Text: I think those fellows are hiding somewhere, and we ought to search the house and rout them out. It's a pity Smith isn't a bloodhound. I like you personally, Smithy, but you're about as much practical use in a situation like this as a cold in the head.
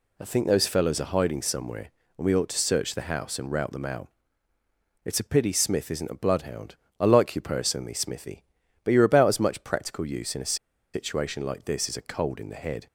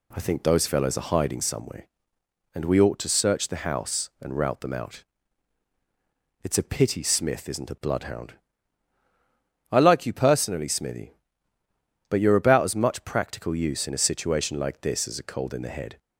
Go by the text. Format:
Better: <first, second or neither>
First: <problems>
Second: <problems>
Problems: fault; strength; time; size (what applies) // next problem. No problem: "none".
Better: second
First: pauses between "a" and "situation"; at 10.5 s; 0.38 s long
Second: none